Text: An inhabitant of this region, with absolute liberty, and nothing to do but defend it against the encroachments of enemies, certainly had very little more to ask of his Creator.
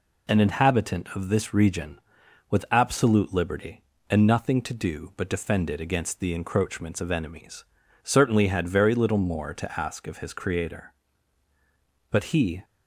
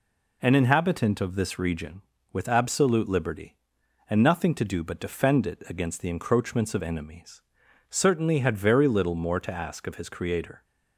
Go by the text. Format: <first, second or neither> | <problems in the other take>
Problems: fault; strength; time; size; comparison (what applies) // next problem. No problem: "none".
second | goes on to say "But he"; from 12.1 s on; 0.54 s long